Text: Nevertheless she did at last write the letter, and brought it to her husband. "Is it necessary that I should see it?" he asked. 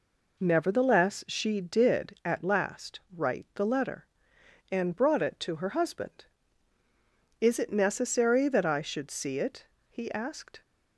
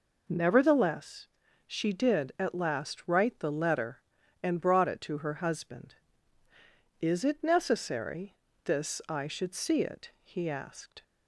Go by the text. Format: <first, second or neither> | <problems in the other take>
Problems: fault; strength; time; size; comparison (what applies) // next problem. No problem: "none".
first | pauses between "Nevertheless" and "she"; at 1.2 s; 0.40 s long // says "this" for "that"; at 8.6 s